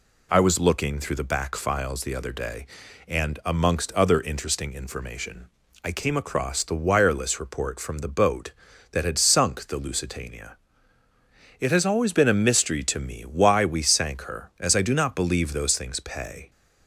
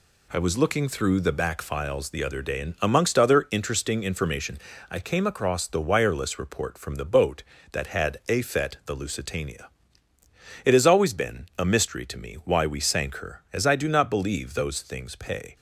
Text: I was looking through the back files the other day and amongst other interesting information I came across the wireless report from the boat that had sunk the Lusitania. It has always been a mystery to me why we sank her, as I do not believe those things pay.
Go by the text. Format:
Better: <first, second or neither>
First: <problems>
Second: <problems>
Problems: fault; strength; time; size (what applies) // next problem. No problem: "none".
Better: first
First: pauses between "information" and "I"; at 5.4 s; 0.38 s long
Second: pauses between "information" and "I"; slight; at 4.5 s; 0.32 s long // says "afet" for "sunk"; at 8.2 s